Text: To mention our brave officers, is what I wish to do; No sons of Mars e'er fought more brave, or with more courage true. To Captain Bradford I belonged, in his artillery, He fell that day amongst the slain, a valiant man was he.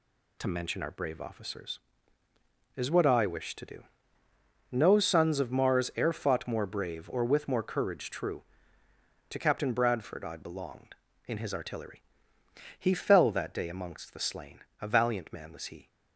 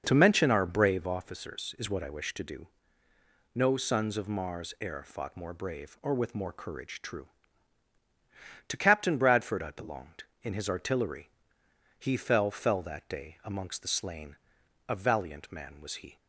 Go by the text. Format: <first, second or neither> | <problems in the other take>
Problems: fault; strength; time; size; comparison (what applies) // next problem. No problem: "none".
first | says "fell" twice; at 12.5 s